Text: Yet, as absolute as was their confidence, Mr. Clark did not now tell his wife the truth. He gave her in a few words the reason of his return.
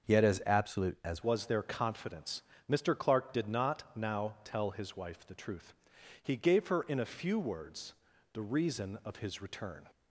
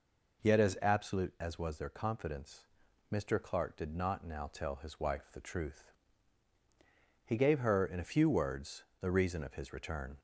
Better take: second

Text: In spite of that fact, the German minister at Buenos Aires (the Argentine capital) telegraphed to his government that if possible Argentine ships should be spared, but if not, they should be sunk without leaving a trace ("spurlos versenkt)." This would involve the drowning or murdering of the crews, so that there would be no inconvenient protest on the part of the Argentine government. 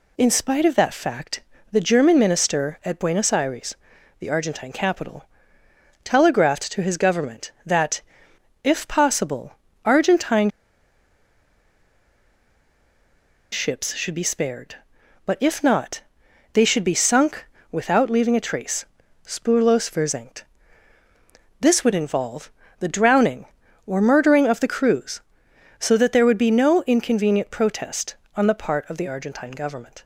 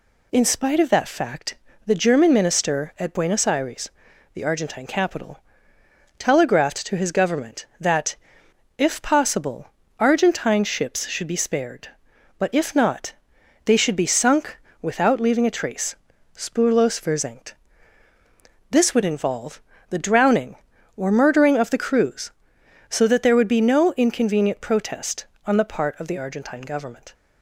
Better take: second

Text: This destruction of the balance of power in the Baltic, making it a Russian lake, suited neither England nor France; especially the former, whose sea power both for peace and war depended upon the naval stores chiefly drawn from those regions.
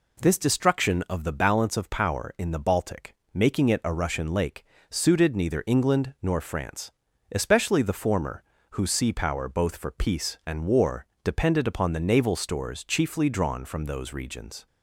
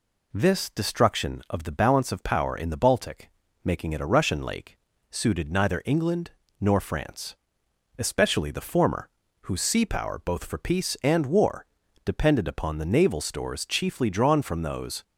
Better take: first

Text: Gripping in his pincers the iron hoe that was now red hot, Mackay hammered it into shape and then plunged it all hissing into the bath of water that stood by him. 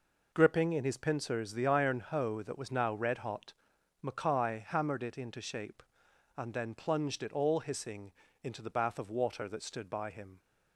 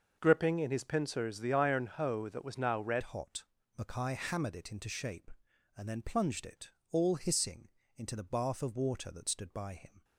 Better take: first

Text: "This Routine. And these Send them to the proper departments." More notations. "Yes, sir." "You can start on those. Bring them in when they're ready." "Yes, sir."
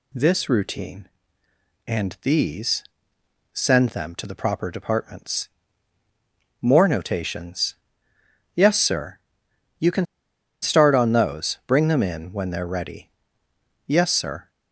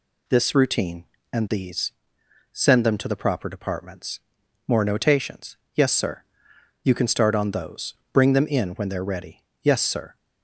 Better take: second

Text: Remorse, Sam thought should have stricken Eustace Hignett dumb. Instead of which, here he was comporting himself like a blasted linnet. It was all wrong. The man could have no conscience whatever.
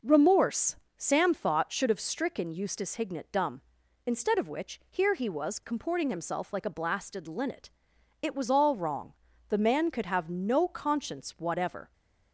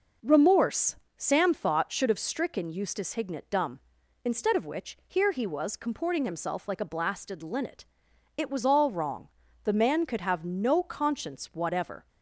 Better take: neither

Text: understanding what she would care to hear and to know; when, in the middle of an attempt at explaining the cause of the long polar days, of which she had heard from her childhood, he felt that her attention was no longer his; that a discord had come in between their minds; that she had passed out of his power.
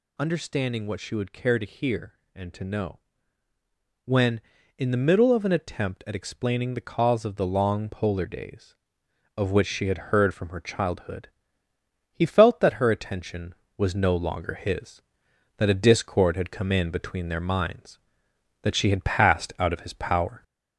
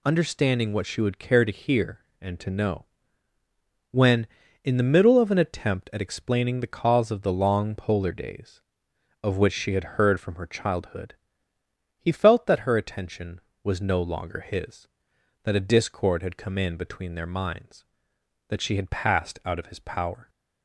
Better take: second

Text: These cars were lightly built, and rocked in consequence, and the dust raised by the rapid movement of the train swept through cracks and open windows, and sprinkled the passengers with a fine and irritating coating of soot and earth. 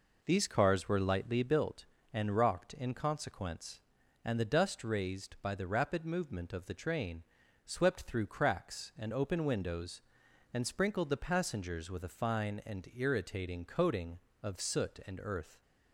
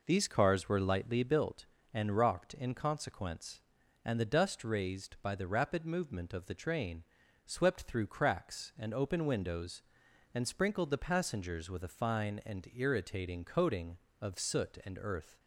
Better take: neither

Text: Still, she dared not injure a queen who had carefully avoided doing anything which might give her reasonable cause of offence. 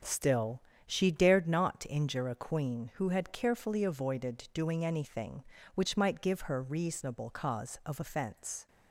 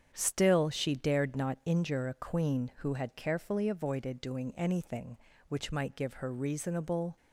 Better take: first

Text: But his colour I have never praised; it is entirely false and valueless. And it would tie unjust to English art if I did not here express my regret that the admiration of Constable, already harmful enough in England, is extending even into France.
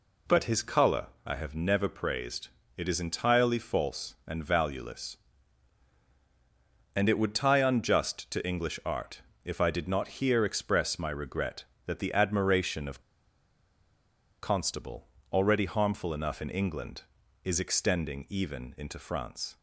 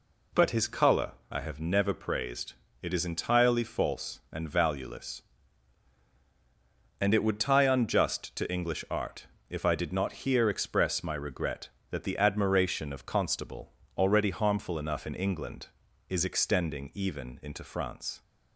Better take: second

